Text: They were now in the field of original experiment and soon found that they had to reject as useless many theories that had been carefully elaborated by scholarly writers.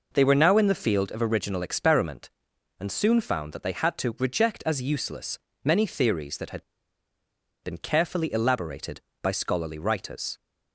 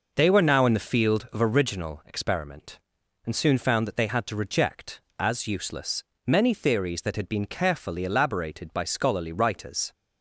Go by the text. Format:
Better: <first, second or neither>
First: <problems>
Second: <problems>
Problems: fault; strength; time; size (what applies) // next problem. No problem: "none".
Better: second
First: pauses between "useless" and "many"; slight; at 5.3 s; 0.26 s long // pauses between "had" and "been"; at 6.6 s; 0.99 s long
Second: pauses between "useless" and "many"; slight; at 6.0 s; 0.24 s long